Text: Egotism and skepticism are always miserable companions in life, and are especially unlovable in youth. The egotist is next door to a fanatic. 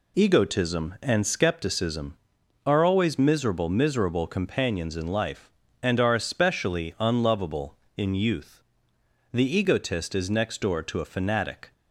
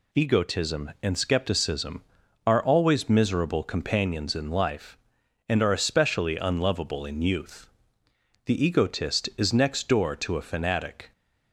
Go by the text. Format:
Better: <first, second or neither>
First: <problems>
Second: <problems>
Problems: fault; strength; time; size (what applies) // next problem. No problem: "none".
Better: second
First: says "miserable" twice; at 3.6 s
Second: none